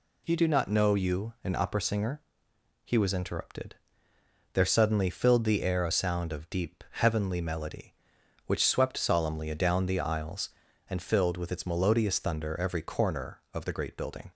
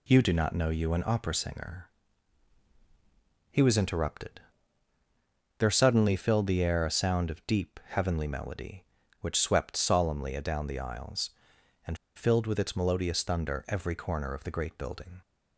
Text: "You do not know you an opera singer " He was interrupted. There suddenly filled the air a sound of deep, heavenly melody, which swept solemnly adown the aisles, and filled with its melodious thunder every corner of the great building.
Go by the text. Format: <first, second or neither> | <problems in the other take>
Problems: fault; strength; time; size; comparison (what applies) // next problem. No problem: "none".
first | pauses between "and" and "filled"; slight; at 11.9 s; 0.18 s long